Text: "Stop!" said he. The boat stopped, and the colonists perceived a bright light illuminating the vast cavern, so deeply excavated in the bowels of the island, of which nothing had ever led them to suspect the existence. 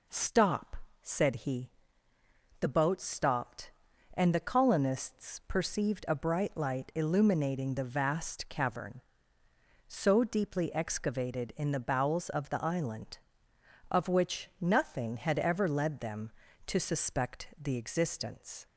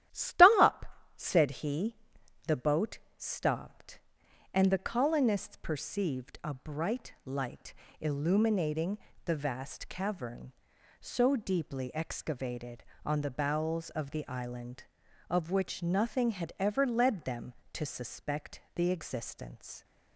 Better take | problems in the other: first | starts louder than the rest; strong; until 1.4 s; 12.5 dB // pauses between "boat" and "stopped"; slight; at 2.9 s; 0.18 s long // pauses between "light" and "illuminating"; slight; at 7.7 s; 0.26 s long // pauses between "illuminating" and "the"; slight; at 8.9 s; 0.28 s long // says "on" for "in"; at 13.0 s

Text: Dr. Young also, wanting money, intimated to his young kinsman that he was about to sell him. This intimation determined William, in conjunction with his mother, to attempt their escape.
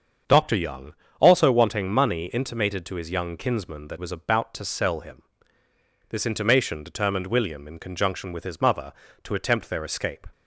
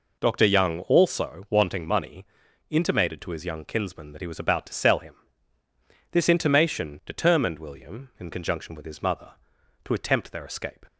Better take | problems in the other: second | starts louder than the rest; until 1.5 s; 7 dB // pauses between "Young" and "also"; slight; at 0.9 s; 0.28 s long // skips "he"; at 3.9 s

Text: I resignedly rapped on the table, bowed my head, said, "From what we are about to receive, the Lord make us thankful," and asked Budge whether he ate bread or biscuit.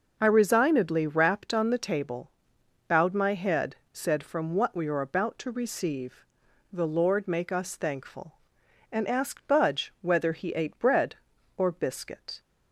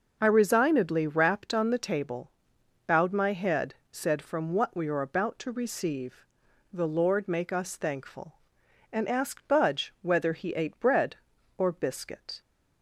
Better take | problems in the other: neither | none

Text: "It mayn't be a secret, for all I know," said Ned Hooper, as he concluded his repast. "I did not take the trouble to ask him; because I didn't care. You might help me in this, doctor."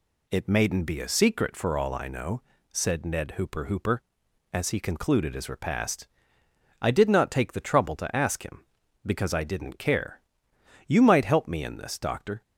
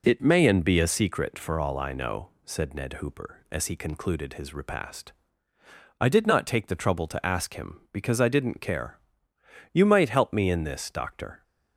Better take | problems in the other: second | says "Hooper" twice; at 3.6 s

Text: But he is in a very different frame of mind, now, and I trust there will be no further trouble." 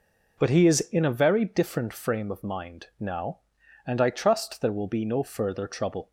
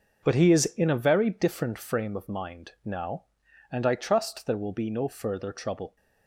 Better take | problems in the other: first | gets quieter; strong; throughout; 8.5 dB

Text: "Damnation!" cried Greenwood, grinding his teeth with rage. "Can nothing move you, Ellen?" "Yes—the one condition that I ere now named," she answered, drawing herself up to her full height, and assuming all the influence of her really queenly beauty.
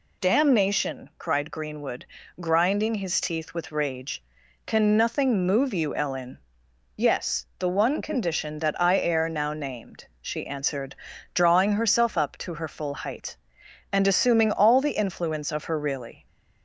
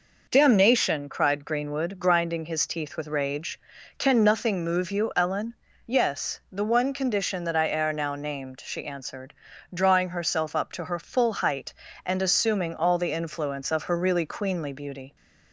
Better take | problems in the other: second | stops before "queenly beauty"; at 16.2 s

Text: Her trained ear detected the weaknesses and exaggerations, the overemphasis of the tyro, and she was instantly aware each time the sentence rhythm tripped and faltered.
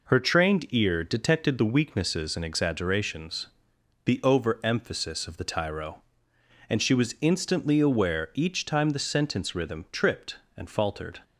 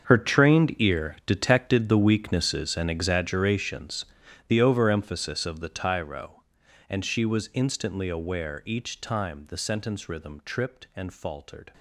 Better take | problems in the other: first | gets quieter; strong; throughout; 15.5 dB

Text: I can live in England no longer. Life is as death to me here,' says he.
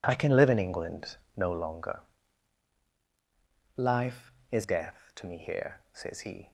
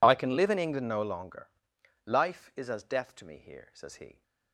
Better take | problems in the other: second | pauses between "England" and "no"; slight; at 1.1 s; 0.18 s long // skips "as"; at 4.6 s

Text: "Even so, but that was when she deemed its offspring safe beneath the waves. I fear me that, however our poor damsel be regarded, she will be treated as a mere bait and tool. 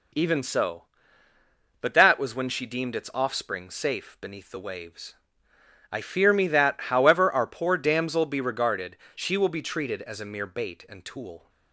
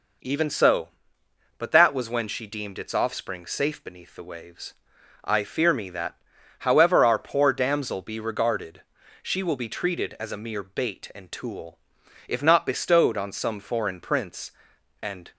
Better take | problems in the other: first | goes on to say "If not bestowed on some foreign prince and"; strong; from 12.2 s on; 3.0 s long

